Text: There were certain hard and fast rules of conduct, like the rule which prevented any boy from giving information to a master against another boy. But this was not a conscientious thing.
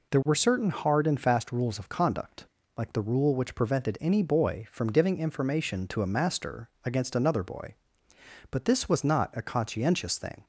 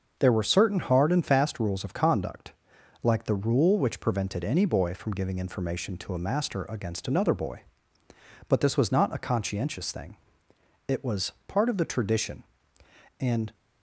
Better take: first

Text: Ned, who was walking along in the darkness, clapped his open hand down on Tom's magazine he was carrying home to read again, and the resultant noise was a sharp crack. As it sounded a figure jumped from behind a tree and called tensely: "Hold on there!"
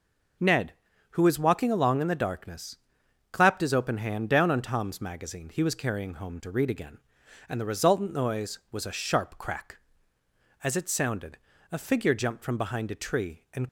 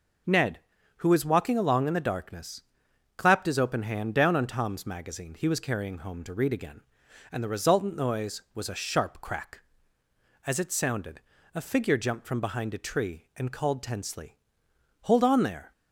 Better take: second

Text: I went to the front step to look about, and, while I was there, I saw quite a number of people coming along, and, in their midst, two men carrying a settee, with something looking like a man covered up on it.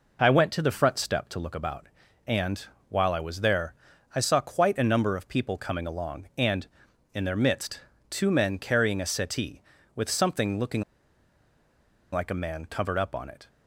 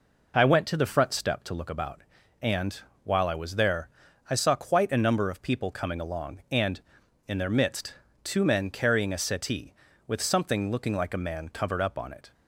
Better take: second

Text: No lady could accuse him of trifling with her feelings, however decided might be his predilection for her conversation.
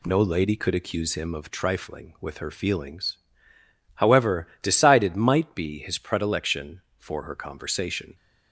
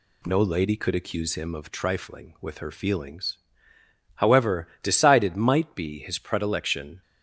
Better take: first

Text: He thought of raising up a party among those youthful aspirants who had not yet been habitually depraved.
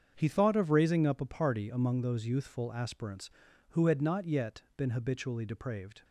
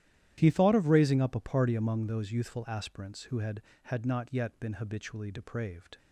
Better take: first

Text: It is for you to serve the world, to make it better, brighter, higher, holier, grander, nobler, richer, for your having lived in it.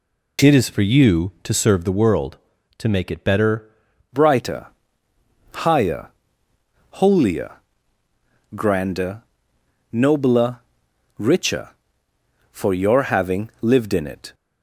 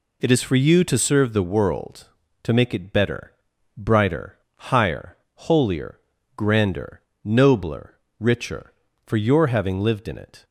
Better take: second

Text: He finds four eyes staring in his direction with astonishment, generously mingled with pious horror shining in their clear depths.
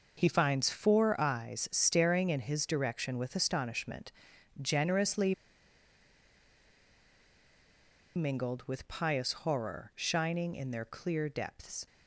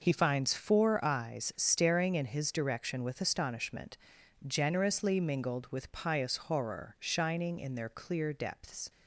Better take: second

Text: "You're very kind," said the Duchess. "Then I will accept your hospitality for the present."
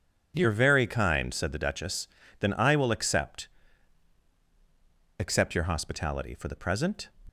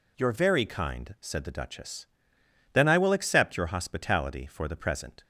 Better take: second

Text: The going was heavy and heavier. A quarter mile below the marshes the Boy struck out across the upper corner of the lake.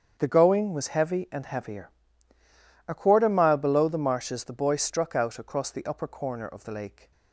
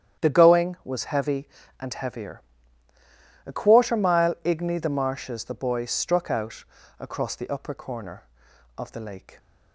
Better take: first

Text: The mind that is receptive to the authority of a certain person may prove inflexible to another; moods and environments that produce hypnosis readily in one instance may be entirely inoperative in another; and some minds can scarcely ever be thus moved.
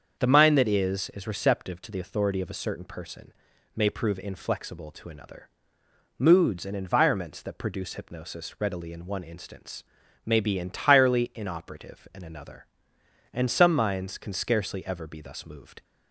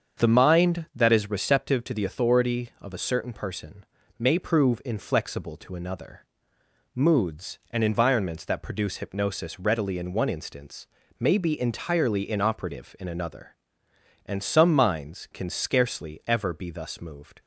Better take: second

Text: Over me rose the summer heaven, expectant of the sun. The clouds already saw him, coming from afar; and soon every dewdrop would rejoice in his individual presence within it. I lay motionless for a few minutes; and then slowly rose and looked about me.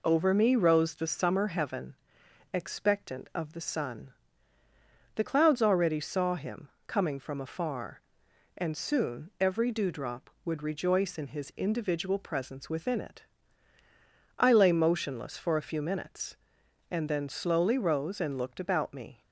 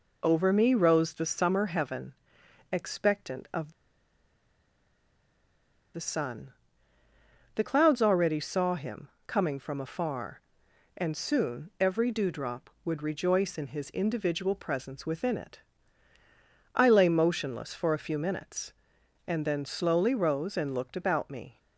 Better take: first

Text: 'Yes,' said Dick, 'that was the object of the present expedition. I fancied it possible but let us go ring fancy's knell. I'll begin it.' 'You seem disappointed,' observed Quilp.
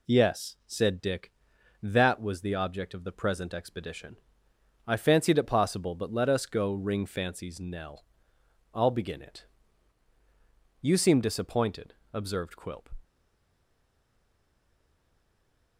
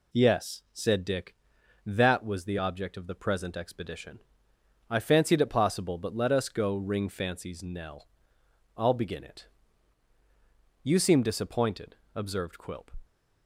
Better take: second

